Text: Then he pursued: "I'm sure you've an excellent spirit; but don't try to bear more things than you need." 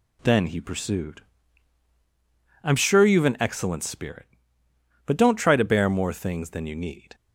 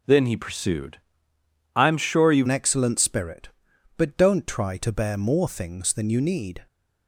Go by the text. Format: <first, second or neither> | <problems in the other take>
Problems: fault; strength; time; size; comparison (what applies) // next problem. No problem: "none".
first | starts louder than the rest; until 1.8 s; 6.5 dB // changes voice at "an"; from 2.4 s on; 4.2 s long